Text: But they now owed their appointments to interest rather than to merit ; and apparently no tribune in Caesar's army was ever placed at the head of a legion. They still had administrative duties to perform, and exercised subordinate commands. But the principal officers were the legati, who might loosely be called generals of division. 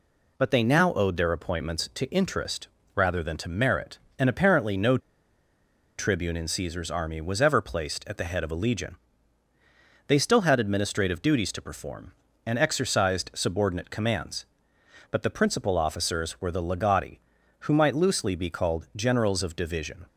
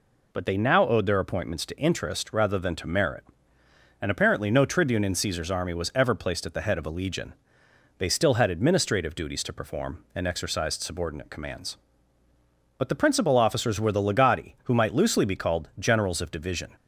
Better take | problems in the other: second | pauses between "interest" and "rather"; slight; at 2.6 s; 0.26 s long // pauses between "no" and "tribune"; at 4.9 s; 1.0 s long

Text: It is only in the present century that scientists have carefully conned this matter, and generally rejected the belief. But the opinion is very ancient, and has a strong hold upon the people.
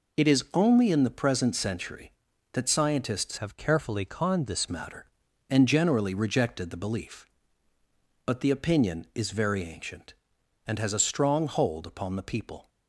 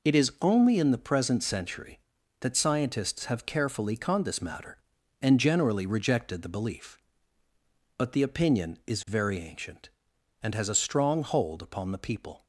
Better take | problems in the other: second | changes voice from "have" to "this"; from 3.3 to 4.6 s; 1.3 s long

